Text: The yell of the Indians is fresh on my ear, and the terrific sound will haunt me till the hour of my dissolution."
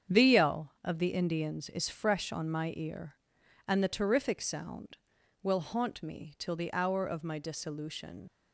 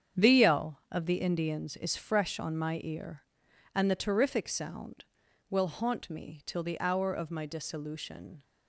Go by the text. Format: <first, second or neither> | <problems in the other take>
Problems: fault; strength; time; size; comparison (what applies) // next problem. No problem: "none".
second | starts louder than the rest; strong; until 1.2 s; 8 dB; strong in the second // leaves "dissolution" unfinished; at 8.2 s; 75 ms